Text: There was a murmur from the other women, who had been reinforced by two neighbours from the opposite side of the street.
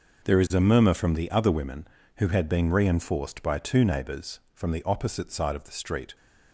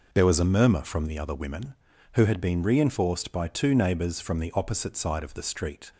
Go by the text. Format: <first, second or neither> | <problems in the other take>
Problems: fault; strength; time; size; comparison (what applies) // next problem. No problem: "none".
second | says "is" for "was"; at 0.4 s